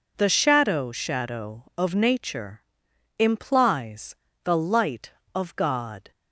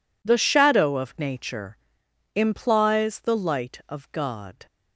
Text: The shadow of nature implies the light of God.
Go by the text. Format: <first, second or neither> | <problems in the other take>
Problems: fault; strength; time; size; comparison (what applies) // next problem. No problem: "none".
second | says "shadow" twice; at 0.9 s // pauses between "nature" and "implies"; noticeable; at 2.6 s; 0.58 s long; noticeable in the second // pauses between "implies" and "the"; slight; at 4.1 s; 0.30 s long